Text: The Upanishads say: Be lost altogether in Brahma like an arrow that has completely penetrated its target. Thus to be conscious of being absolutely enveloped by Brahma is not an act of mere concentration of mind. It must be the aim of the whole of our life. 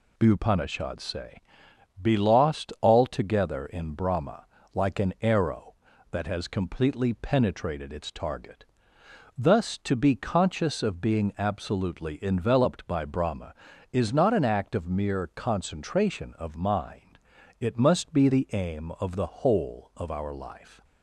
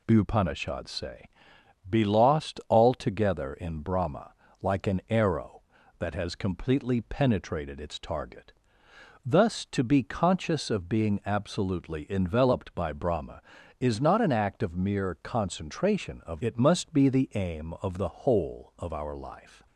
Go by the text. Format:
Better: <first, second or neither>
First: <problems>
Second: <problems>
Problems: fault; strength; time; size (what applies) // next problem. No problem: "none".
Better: first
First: pauses between "Brahma" and "like"; slight; at 4.4 s; 0.28 s long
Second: pauses between "Brahma" and "like"; slight; at 4.3 s; 0.28 s long // skips "mind"; at 16.4 s